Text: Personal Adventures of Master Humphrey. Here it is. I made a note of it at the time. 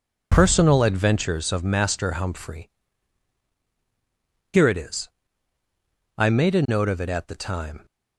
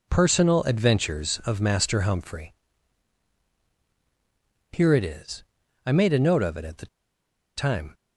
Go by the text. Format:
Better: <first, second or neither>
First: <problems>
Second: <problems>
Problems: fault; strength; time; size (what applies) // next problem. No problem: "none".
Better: first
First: none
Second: pauses between "the" and "time"; noticeable; at 6.8 s; 0.69 s long